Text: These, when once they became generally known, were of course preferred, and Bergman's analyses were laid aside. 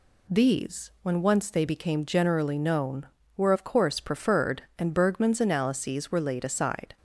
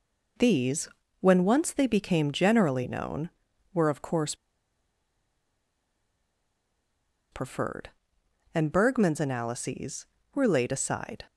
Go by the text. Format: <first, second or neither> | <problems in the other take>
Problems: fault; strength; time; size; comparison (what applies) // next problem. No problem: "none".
first | pauses between "course" and "preferred"; strong; at 4.3 s; 2.9 s long